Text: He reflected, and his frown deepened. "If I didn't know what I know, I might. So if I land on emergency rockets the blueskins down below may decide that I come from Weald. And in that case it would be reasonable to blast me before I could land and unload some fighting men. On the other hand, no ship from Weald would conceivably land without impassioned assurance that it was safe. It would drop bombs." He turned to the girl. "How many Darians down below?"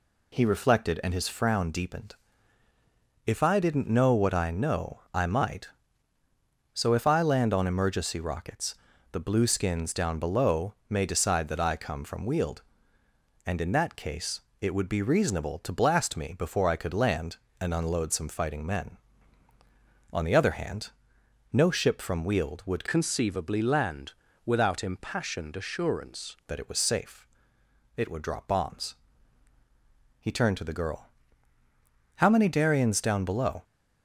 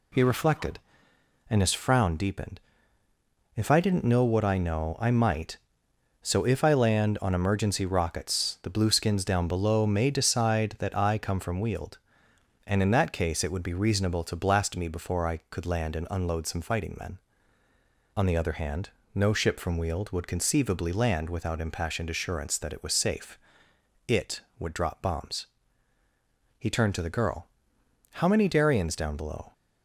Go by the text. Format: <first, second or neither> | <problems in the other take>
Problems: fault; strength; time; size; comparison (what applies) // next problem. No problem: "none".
second | pauses between "rockets" and "the"; at 8.7 s; 0.38 s long // pauses between "below" and "may"; slight; at 10.7 s; 0.16 s long // pauses between "case" and "it"; slight; at 14.4 s; 0.18 s long // changes voice from "conceivably" to "assurance"; from 22.8 to 26.3 s; 3.5 s long // pauses between "land" and "without"; slight; at 24.1 s; 0.34 s long